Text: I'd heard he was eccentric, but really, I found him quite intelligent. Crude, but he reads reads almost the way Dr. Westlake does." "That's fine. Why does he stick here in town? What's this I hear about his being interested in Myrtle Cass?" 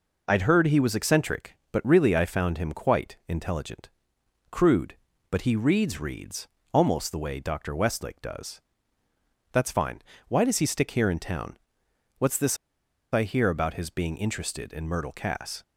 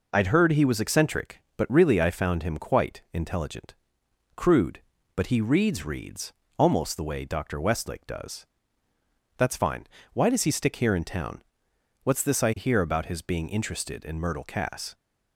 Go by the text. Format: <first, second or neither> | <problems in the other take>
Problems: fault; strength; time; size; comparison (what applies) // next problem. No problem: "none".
second | pauses between "reads" and "almost"; slight; at 6.4 s; 0.26 s long; slight in the second // pauses between "this" and "I"; noticeable; at 12.5 s; 0.57 s long